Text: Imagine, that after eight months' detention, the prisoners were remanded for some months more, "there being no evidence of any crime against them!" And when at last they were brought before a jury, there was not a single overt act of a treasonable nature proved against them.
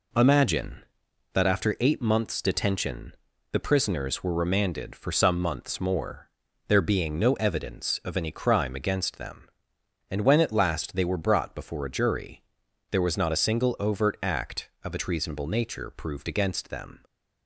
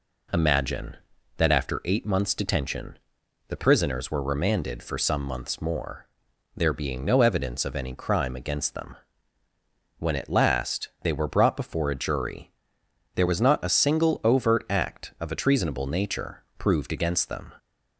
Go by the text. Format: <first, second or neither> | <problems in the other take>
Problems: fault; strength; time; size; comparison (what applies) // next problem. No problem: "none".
first | skips "And"; at 9.4 s // pauses between "nature" and "proved"; slight; at 16.4 s; 0.16 s long